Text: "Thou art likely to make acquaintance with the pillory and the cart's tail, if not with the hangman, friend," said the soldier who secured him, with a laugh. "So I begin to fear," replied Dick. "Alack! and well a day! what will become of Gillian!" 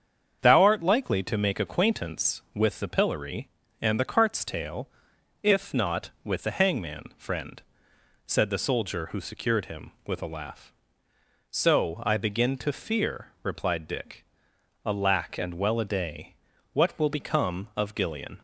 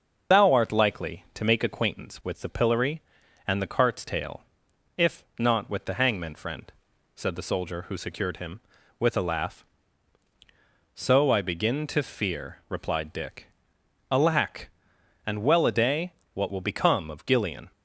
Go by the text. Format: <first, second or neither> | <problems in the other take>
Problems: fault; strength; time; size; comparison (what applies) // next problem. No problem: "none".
first | loses the start of "Thou"; at 0.3 s; 45 ms // starts louder than the rest; until 1.4 s; 6.5 dB; strong in the first // pauses between "if" and "not"; slight; at 5.2 s; 0.16 s long